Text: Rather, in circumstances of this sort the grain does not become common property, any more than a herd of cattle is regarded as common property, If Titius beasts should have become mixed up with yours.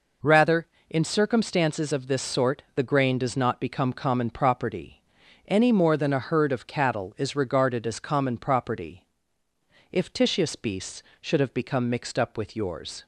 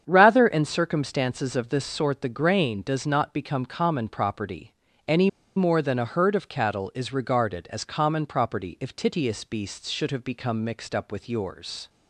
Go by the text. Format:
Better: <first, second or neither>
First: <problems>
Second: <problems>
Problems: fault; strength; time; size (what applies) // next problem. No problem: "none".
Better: first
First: none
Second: starts louder than the rest; strong; until 1.0 s; 8 dB // pauses between "any" and "more"; slight; at 5.2 s; 0.27 s long